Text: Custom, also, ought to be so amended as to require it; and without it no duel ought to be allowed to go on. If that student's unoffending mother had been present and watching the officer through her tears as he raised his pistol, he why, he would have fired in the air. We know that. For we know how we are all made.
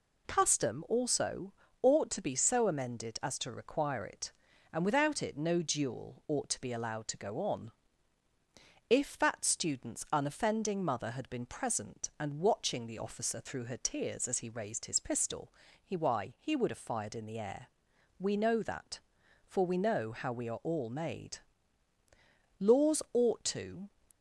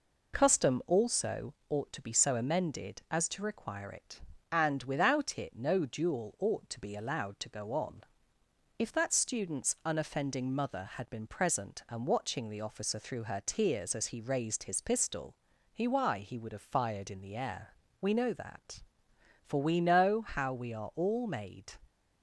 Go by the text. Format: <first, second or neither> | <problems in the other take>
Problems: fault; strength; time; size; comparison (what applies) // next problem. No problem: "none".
second | goes on to say "Laws ought to"; from 22.5 s on; 1.3 s long